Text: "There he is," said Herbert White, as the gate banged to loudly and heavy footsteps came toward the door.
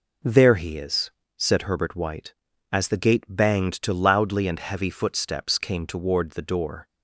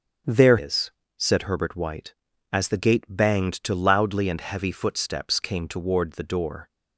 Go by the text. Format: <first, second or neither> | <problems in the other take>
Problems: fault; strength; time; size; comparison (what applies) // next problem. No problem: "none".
first | starts louder than the rest; strong; until 1.5 s; 7.5 dB // skips "he"; at 0.5 s